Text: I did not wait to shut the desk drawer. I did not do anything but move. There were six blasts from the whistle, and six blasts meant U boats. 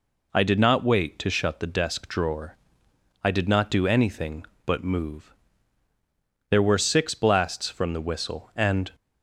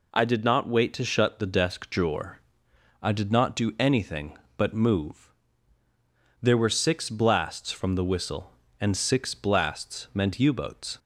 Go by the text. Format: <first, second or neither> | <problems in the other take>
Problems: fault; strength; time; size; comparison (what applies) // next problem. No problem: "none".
second | stops before "six blasts meant U boats"; at 8.9 s